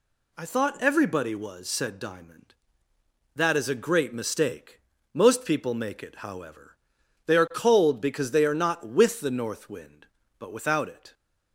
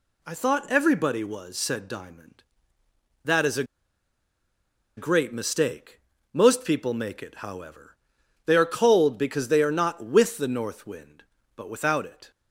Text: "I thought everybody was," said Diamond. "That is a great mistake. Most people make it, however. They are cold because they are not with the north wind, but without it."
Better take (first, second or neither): first